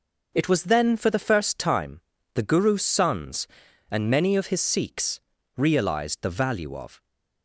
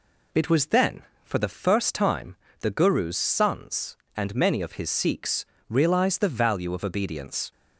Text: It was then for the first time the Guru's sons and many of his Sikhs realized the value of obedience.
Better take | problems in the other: second | pauses between "time" and "the"; slight; at 2.0 s; 0.34 s long; slight in the second // pauses between "Sikhs" and "realized"; slight; at 5.2 s; 0.36 s long; slight in the second // stops before "obedience"; at 7.0 s

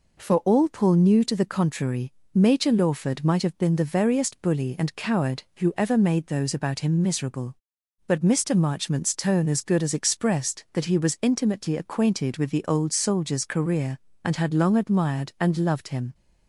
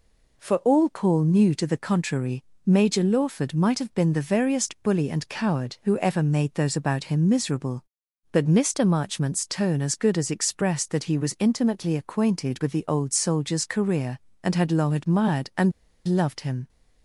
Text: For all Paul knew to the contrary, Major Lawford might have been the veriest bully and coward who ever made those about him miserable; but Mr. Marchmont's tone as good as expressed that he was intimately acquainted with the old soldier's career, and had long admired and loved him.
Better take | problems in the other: first | pauses between "and" and "loved"; slight; at 15.7 s; 0.34 s long

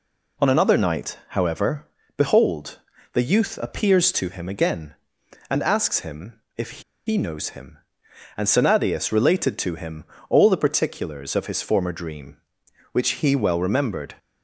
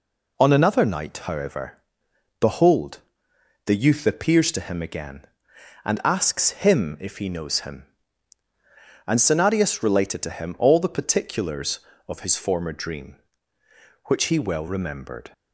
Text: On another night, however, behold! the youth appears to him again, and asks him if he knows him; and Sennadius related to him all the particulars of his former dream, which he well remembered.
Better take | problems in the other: second | pauses between "him" and "if"; slight; at 6.3 s; 0.20 s long // pauses between "if" and "he"; slight; at 6.8 s; 0.24 s long // pauses between "him" and "all"; slight; at 10.0 s; 0.24 s long

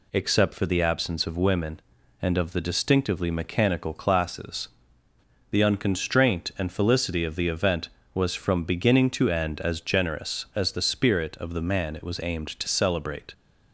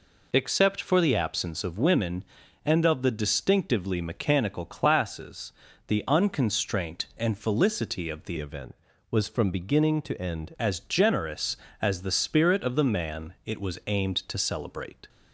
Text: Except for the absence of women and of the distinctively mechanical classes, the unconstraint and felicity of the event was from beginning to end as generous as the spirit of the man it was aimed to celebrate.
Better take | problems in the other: first | changes voice from "event" to "end"; from 8.3 to 10.5 s; 2.2 s long

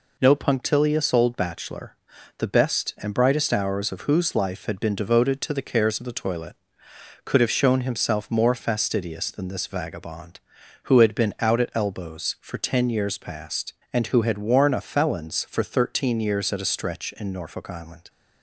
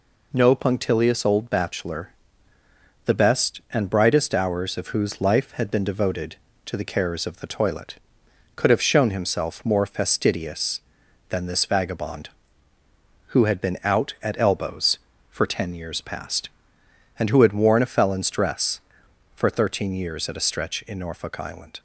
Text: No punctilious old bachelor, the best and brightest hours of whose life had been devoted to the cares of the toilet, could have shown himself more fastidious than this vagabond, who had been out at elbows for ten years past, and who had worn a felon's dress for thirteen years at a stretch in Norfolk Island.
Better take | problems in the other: second | skips "dress"; at 15.4 s

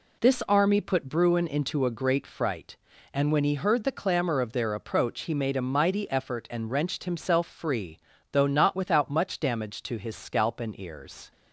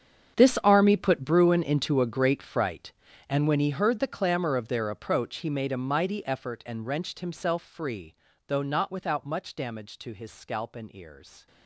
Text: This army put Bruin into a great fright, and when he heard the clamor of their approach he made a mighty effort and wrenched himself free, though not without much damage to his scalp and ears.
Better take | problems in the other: first | gets quieter; strong; throughout; 17.5 dB

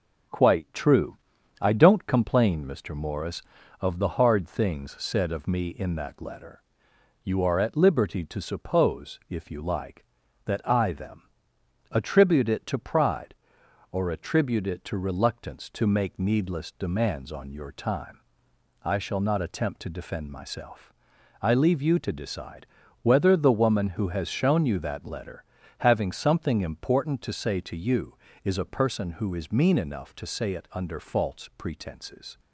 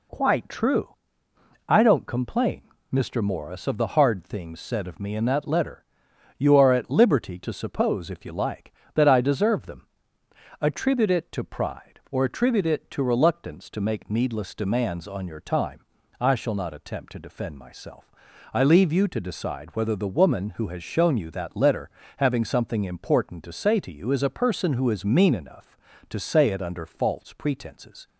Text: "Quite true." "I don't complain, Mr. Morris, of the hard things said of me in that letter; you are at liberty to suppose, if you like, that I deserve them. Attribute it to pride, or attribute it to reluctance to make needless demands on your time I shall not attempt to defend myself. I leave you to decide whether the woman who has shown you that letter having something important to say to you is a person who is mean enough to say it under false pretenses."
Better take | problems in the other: second | skips "deserve"; at 10.9 s // pauses between "time" and "I"; noticeable; at 18.1 s; 0.64 s long; slight in the second // pauses between "decide" and "whether"; slight; at 22.6 s; 0.34 s long // pauses between "letter" and "having"; slight; at 25.4 s; 0.36 s long; slight in the second

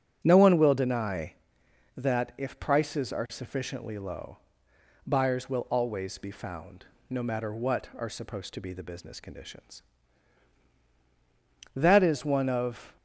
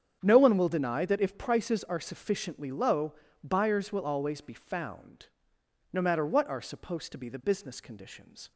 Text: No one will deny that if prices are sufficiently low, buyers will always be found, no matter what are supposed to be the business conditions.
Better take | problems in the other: second | starts louder than the rest; strong; until 1.2 s; 8.5 dB; strong in the second // goes on to say "That is one of"; noticeable; from 11.7 s on; 1.2 s long

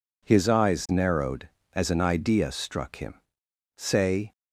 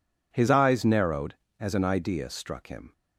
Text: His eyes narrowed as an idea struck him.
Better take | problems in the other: second | goes on to say "Say"; from 3.7 s on; 0.56 s long

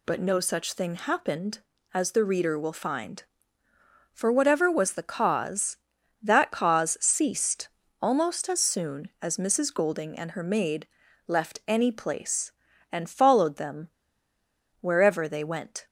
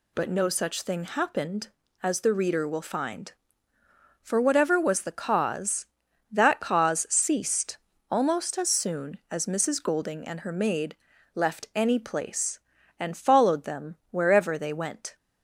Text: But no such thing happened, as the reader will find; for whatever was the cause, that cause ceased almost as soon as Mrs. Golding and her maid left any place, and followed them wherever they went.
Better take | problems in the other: second | pauses between "ceased" and "almost"; slight; at 7.6 s; 0.34 s long; slight in the second // pauses between "maid" and "left"; at 10.8 s; 0.40 s long; also in the second // pauses between "them" and "wherever"; noticeable; at 13.8 s; 0.91 s long

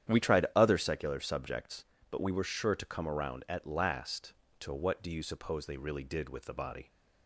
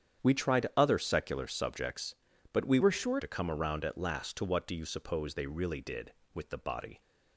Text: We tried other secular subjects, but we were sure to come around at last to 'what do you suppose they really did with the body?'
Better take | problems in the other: first | starts louder than the rest; strong; until 1.3 s; 9 dB; strong in the first // changes voice from "were" to "sure"; from 2.8 to 3.1 s; 0.3 s long

